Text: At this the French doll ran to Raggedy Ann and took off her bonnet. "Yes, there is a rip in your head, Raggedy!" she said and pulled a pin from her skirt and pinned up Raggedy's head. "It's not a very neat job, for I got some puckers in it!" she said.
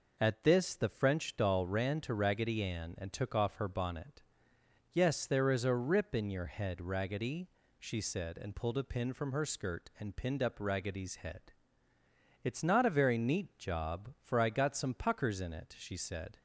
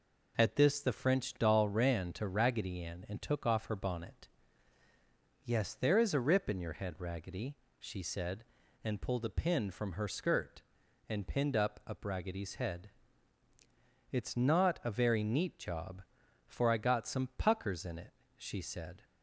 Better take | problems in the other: first | says "up" twice; at 11.8 s

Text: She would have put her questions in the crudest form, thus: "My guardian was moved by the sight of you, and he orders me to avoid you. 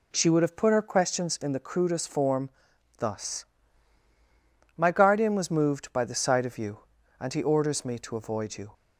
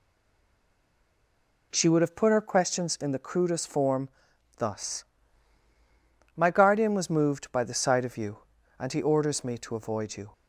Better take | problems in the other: first | stays silent before the first word; noticeable; until 1.7 s; 1.7 s long

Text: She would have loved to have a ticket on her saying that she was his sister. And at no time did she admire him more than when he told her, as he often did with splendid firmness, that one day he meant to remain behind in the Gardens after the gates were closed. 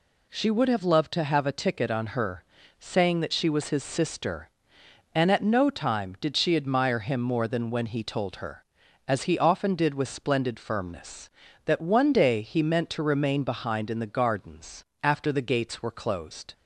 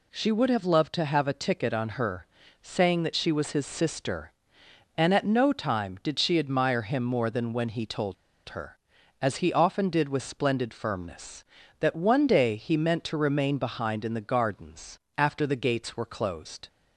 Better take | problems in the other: first | pauses between "her" and "saying"; slight; at 2.2 s; 0.36 s long; slight in the first // pauses between "told" and "her"; slight; at 8.1 s; 0.34 s long // pauses between "Gardens" and "after"; slight; at 14.9 s; 0.18 s long; slight in the first

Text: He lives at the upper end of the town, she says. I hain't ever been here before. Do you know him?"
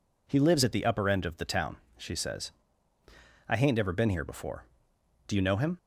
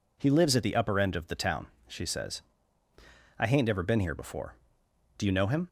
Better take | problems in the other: neither | none

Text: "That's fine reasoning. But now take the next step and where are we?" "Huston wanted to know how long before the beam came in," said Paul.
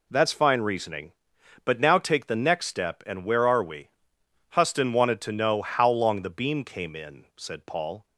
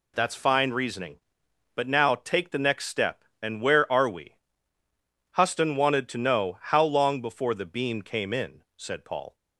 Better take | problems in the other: second | skips "before"; at 6.2 s

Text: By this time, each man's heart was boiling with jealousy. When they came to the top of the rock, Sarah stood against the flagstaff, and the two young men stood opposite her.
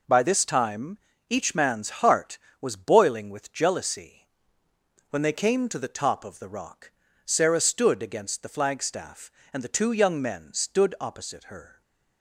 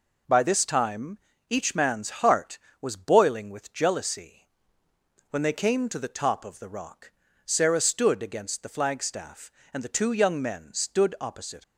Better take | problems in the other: first | stops before "her"; at 11.6 s

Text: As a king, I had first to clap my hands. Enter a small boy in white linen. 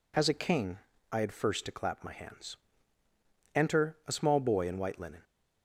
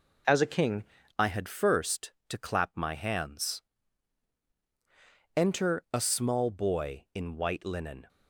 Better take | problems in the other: first | changes voice at "I"; from 1.1 s on; 6.9 s long

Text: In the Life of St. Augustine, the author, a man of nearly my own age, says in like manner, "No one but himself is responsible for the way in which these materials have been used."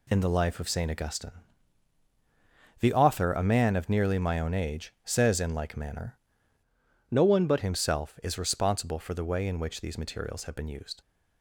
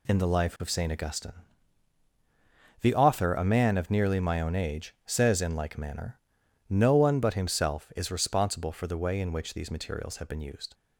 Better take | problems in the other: second | changes voice from "No" to "but"; from 7.0 to 7.6 s; 0.6 s long

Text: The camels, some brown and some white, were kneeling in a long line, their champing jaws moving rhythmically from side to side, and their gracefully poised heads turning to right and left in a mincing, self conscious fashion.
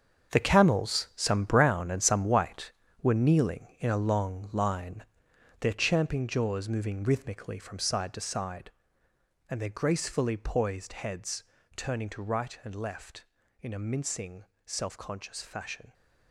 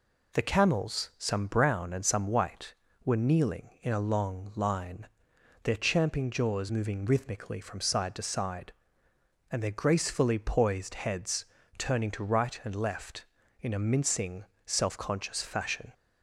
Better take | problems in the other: second | gets quieter; strong; throughout; 11 dB // pauses between "heads" and "turning"; slight; at 11.4 s; 0.32 s long; slight in the second

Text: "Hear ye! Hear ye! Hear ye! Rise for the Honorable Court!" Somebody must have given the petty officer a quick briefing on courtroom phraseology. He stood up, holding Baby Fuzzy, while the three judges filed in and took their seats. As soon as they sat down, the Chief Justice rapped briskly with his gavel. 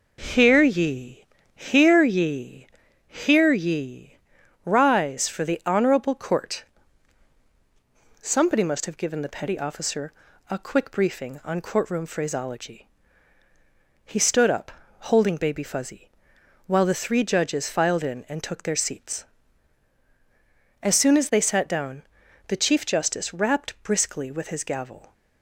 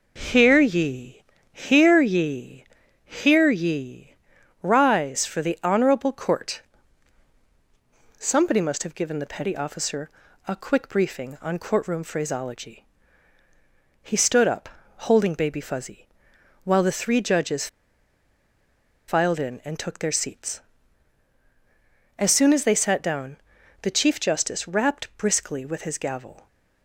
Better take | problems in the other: first | pauses between "officer" and "a"; at 10.0 s; 0.38 s long; also in the first // pauses between "judges" and "filed"; strong; at 17.6 s; 1.4 s long

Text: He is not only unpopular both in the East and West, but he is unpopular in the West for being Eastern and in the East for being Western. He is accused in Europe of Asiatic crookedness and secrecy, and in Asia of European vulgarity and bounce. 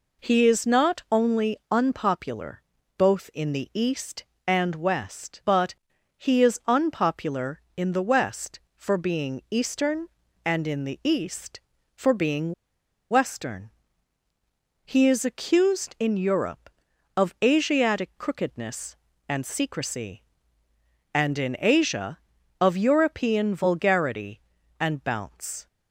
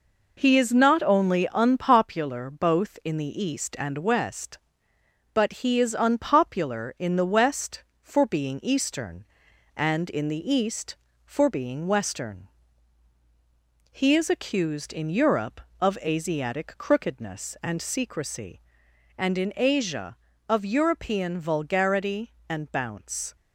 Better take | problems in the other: second | pauses between "unpopular" and "both"; slight; at 2.6 s; 0.36 s long // pauses between "but" and "he"; at 5.7 s; 0.44 s long // pauses between "being" and "Western"; noticeable; at 12.5 s; 0.58 s long

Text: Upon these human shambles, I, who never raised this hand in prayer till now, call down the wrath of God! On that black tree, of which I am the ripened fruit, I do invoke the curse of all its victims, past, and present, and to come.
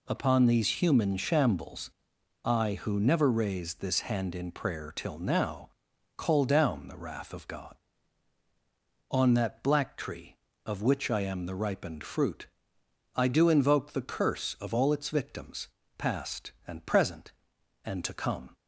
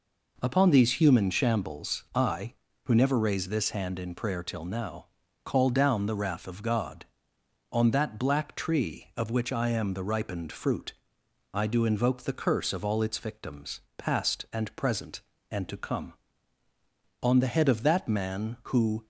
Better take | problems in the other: first | goes on to say "On the head of that man who"; strong; from 17.2 s on; 1.8 s long

